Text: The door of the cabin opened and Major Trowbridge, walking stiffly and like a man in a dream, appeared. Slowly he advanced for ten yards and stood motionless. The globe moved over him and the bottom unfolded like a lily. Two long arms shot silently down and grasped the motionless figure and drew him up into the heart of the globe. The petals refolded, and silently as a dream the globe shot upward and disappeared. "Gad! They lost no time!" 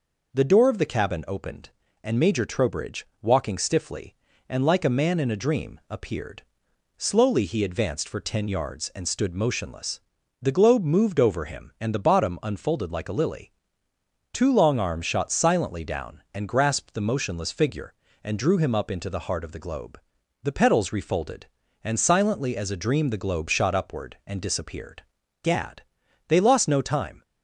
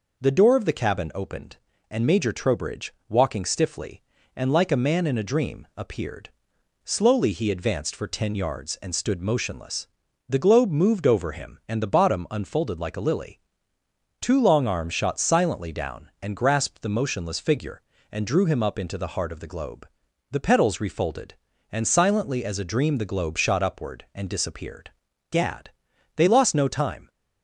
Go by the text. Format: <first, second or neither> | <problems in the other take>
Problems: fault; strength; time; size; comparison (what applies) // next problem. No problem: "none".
neither | none